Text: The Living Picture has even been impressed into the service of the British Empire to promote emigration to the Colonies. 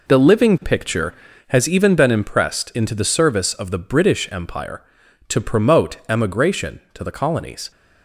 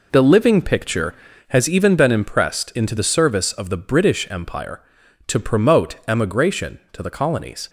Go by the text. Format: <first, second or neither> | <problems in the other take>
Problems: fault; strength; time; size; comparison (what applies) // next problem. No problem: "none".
neither | none